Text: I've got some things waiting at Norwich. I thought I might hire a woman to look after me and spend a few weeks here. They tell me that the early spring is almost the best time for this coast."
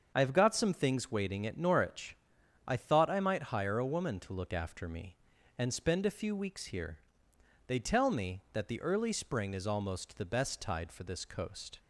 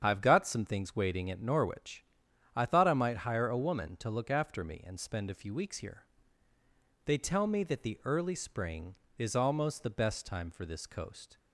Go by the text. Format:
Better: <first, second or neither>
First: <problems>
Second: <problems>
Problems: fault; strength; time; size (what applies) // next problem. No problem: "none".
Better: second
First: starts louder than the rest; until 1.1 s; 6.5 dB // says "tide" for "time"; at 10.5 s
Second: starts louder than the rest; strong; until 1.0 s; 8 dB